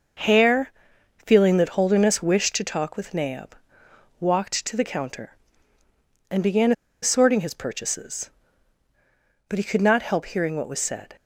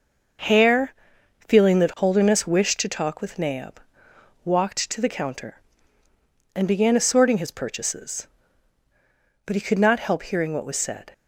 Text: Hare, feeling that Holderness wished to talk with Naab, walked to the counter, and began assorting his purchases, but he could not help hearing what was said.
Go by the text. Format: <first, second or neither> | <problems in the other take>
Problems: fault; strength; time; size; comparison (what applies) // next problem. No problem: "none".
second | pauses between "began" and "assorting"; slight; at 6.7 s; 0.30 s long